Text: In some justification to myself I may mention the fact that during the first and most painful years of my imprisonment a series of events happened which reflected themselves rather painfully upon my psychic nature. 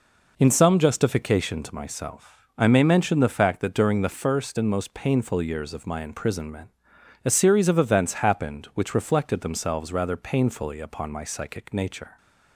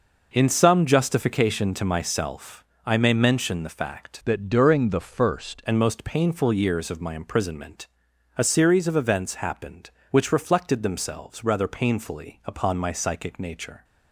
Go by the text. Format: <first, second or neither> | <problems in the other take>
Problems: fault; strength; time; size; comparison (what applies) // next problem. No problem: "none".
first | pauses between "myself" and "I"; slight; at 2.6 s; 0.22 s long // changes voice from "that" to "first"; from 4.2 to 5.6 s; 1.4 s long // pauses between "imprisonment" and "a"; noticeable; at 7.8 s; 0.50 s long; noticeable in the first